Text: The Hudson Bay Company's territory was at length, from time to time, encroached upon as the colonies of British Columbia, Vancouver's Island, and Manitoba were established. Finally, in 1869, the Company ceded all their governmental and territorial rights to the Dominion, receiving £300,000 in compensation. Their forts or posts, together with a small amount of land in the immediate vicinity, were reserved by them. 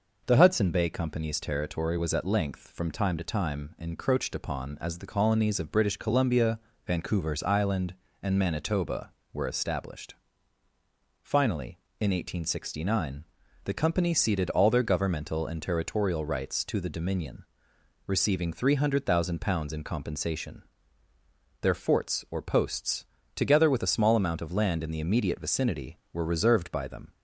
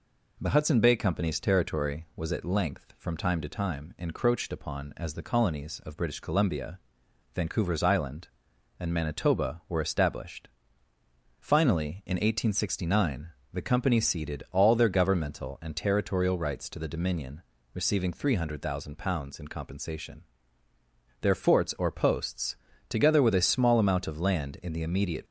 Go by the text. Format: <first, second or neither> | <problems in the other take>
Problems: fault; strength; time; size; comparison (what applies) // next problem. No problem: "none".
first | stops before "vicinity were reserved by them"; at 25.2 s